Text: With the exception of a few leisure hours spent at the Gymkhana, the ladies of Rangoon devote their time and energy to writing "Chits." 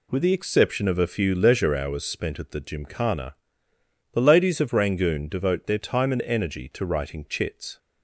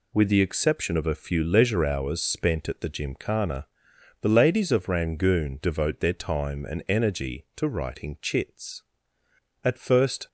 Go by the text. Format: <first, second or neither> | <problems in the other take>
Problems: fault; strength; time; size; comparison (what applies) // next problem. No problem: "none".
first | goes on to say "At first"; noticeable; from 9.6 s on; 0.64 s long